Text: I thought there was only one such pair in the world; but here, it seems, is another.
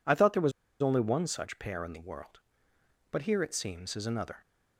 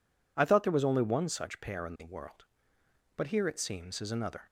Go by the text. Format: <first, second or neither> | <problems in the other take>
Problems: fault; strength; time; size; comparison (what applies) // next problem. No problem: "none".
second | pauses between "was" and "only"; slight; at 0.5 s; 0.31 s long